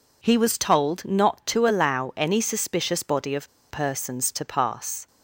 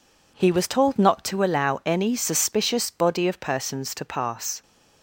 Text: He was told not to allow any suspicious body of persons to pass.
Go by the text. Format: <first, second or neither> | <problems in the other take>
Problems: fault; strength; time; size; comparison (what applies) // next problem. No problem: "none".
second | pauses between "of" and "persons"; slight; at 3.4 s; 0.22 s long